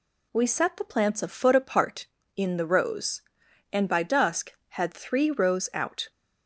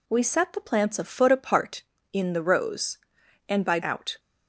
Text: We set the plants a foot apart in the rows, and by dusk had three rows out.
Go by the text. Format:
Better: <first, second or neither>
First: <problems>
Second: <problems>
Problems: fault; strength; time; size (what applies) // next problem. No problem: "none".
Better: first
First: none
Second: skips "dusk had three rows"; at 3.8 s